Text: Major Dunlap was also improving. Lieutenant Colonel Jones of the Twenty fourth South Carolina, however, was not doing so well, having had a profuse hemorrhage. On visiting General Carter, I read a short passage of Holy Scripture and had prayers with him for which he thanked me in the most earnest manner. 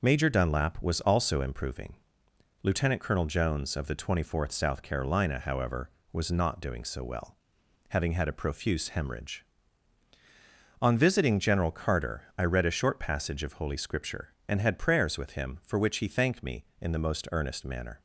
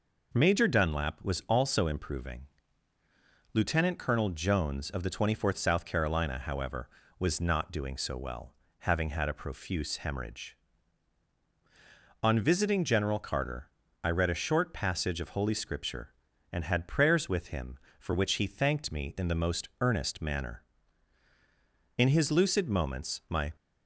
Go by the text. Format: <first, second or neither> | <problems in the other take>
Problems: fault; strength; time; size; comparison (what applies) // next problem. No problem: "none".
first | goes on to say "In his lucid moments my"; from 21.9 s on; 1.5 s long